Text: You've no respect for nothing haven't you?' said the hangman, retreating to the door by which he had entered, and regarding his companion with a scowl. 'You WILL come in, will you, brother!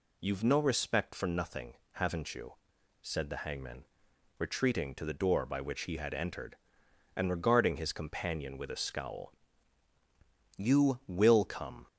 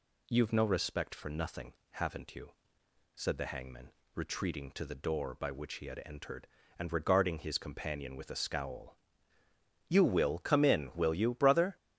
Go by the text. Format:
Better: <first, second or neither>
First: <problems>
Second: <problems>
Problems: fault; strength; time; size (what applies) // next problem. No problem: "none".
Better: second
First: pauses between "nothing" and "haven't"; slight; at 1.7 s; 0.20 s long // stops before "in will you brother"; at 11.8 s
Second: pauses between "nothing" and "haven't"; slight; at 1.7 s; 0.18 s long